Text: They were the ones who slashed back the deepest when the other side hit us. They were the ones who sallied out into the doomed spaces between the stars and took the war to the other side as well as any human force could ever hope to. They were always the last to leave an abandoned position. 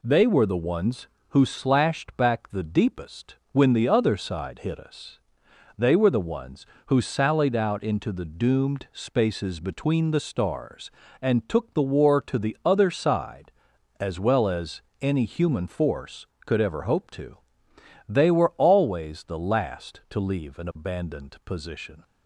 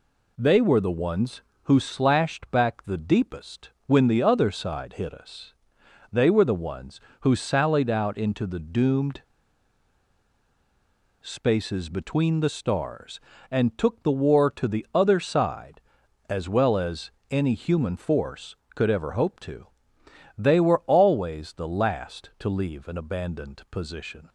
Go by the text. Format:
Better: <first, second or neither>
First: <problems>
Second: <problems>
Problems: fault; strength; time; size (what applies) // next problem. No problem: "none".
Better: first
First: pauses between "deepest" and "when"; slight; at 3.3 s; 0.16 s long // pauses between "as" and "any"; slight; at 14.8 s; 0.20 s long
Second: pauses between "deepest" and "when"; slight; at 3.6 s; 0.16 s long // pauses between "doomed" and "spaces"; strong; at 9.2 s; 2.0 s long // pauses between "as" and "any"; slight; at 17.1 s; 0.20 s long